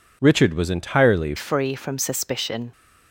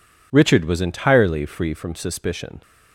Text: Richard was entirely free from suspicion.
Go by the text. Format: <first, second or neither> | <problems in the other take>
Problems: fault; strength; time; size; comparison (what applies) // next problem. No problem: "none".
second | changes voice at "free"; from 1.3 s on; 1.4 s long